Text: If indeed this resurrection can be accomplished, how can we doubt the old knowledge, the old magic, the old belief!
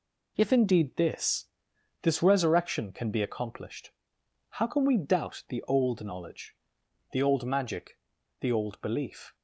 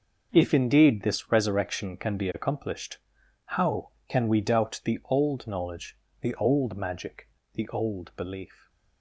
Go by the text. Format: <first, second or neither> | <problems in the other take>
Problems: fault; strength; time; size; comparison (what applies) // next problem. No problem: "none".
second | says "this" twice; at 2.0 s